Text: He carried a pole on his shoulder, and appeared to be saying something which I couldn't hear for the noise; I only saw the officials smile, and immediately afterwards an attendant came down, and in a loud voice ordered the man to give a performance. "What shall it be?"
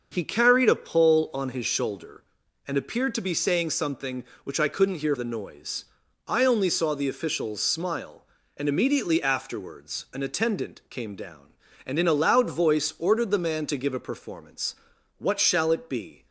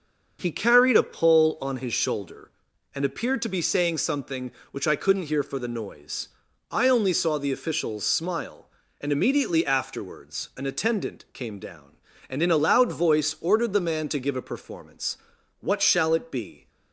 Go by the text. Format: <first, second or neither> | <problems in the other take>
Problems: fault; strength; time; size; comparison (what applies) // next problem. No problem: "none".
second | starts louder than the rest; until 1.1 s; 6.5 dB; also in the second // skips "for"; at 5.1 s